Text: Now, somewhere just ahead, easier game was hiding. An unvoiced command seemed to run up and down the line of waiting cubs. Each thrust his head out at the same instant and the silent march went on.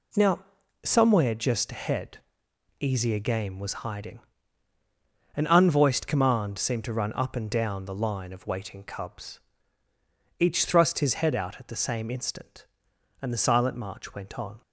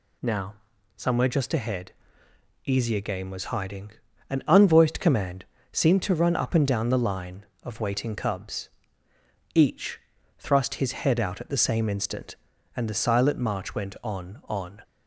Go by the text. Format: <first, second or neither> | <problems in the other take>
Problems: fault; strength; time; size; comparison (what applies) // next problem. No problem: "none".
first | pauses between "command" and "seemed"; slight; at 5.4 s; 0.26 s long // pauses between "Each" and "thrust"; at 9.9 s; 0.40 s long // says "on" twice; at 14.4 s